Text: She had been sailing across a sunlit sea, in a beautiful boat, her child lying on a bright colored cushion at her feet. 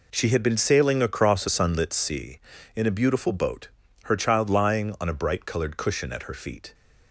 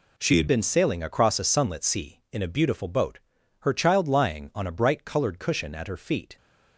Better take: first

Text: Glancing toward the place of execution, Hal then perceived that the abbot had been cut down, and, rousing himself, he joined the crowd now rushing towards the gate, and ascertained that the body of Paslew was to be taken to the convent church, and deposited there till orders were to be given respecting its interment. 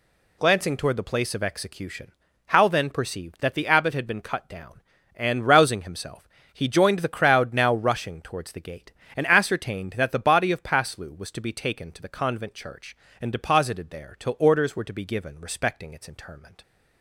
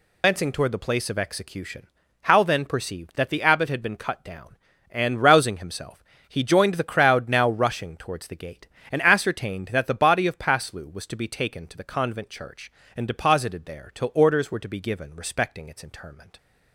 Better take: first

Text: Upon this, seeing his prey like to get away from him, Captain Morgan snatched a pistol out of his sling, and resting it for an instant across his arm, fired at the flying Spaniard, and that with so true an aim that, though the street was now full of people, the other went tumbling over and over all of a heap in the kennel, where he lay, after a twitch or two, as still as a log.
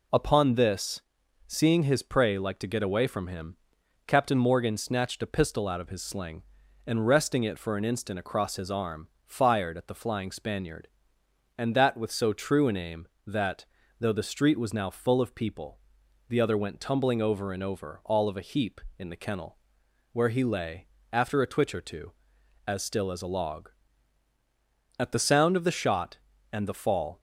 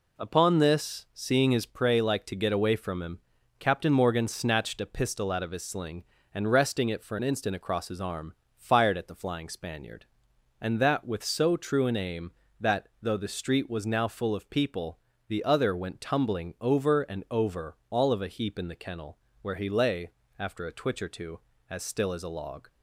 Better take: second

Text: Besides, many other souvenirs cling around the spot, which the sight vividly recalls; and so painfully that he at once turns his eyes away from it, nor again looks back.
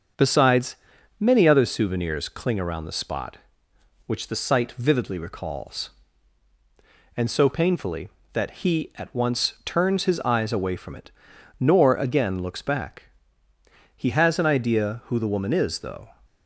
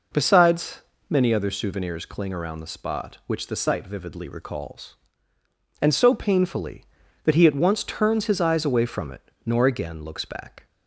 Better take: second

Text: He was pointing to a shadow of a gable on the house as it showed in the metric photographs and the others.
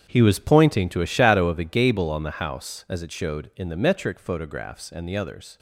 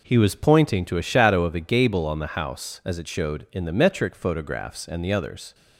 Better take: second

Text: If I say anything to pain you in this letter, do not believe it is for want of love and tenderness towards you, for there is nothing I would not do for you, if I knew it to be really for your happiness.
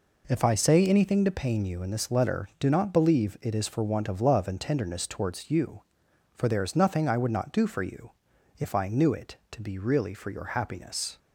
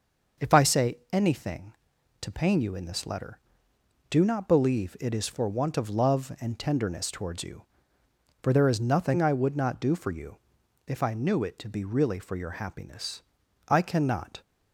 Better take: first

